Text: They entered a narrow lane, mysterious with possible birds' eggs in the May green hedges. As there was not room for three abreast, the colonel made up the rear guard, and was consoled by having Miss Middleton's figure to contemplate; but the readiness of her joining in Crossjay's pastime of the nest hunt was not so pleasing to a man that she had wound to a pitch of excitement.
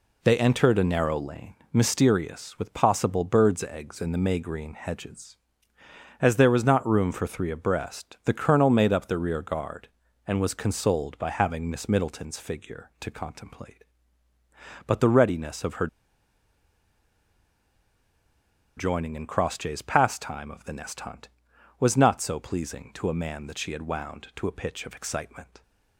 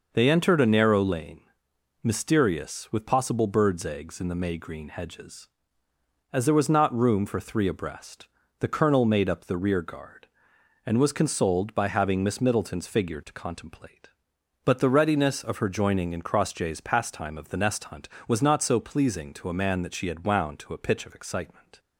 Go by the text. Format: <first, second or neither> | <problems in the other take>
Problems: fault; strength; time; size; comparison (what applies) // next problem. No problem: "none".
second | pauses between "her" and "joining"; strong; at 15.8 s; 2.9 s long